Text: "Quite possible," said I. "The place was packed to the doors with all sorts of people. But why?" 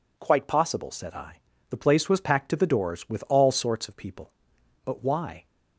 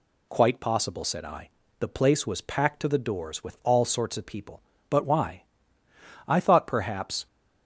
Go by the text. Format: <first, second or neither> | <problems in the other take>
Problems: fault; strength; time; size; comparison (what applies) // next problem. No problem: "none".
first | goes on to say "I thought perhaps"; noticeable; from 6.2 s on; 1.0 s long